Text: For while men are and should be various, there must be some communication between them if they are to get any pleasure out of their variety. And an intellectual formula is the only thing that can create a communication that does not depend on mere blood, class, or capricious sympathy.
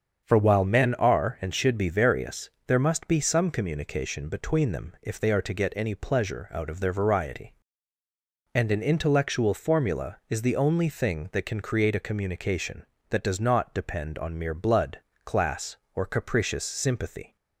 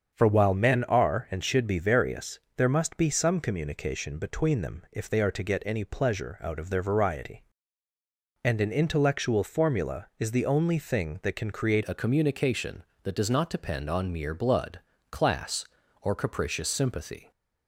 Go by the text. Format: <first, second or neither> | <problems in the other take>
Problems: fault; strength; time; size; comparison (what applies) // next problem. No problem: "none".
first | starts louder than the rest; strong; until 1.1 s; 7 dB; strong in the first // changes voice at "a"; from 11.8 s on; 5.5 s long